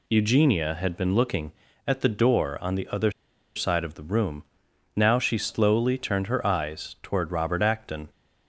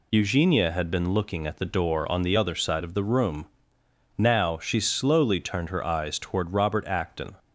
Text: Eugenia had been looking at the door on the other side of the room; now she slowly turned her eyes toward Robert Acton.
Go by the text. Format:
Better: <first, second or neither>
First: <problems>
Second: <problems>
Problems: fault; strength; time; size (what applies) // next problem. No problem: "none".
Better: second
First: pauses between "other" and "side"; at 3.1 s; 0.45 s long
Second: none